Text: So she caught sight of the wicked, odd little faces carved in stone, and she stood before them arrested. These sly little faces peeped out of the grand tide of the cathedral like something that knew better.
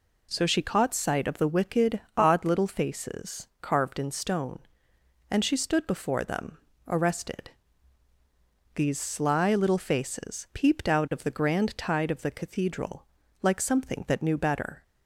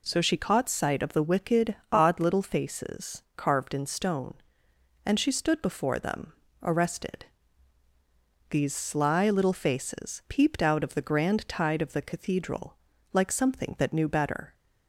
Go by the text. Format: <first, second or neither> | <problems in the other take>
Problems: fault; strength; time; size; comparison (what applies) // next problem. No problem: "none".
neither | pauses between "them" and "arrested"; slight; the same in both // pauses between "cathedral" and "like"; the same in both